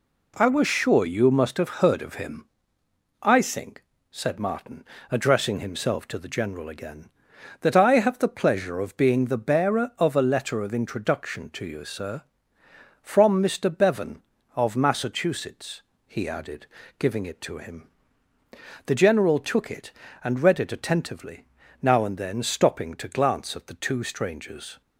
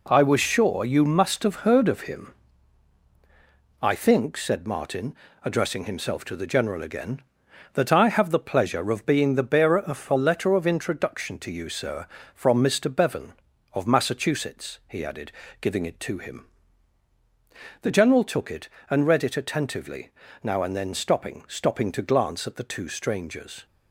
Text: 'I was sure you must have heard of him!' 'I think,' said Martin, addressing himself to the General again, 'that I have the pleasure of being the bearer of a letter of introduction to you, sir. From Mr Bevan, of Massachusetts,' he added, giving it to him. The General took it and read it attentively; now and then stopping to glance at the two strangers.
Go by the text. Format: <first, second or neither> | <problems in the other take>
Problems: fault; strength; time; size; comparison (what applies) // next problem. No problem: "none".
first | says "stopping" twice; at 21.4 s